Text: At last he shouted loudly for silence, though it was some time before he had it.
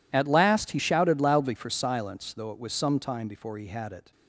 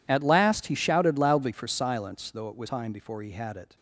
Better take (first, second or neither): first